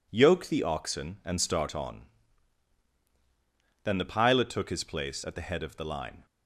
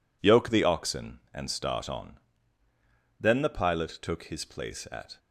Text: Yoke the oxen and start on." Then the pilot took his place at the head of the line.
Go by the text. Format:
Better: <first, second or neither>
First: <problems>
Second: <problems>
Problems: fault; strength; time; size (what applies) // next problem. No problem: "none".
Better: first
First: none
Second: stops before "the head of the line"; at 5.1 s